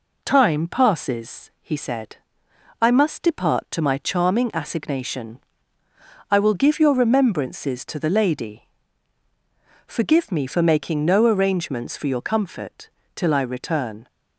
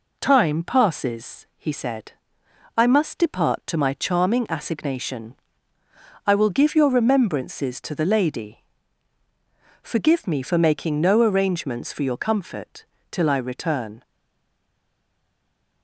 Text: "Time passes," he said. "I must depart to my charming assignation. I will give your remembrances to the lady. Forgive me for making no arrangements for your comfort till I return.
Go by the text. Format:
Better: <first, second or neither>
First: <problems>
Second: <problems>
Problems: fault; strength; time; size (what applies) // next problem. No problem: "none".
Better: first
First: pauses between "comfort" and "till"; slight; at 12.8 s; 0.28 s long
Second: pauses between "comfort" and "till"; slight; at 12.8 s; 0.28 s long // stays silent after the last word; noticeable; from 14.0 s on; 1.8 s long